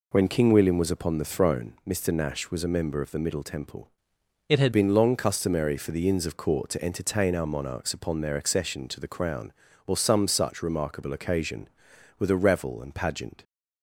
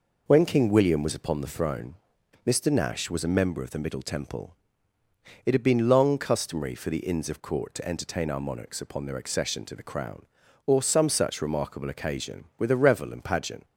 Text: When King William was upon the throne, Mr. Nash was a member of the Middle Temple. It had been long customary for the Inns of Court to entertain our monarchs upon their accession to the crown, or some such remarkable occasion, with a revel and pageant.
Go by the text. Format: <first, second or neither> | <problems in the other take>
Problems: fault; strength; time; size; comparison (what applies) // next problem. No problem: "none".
second | changes voice from "It" to "had"; from 4.4 to 4.7 s; 0.3 s long